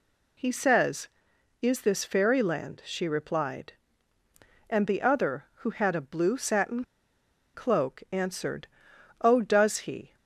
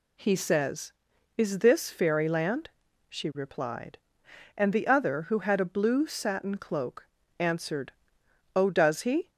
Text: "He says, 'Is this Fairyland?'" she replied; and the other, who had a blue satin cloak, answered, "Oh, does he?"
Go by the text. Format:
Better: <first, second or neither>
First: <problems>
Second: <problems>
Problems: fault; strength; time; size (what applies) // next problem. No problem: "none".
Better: second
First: pauses between "satin" and "cloak"; noticeable; at 6.8 s; 0.71 s long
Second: none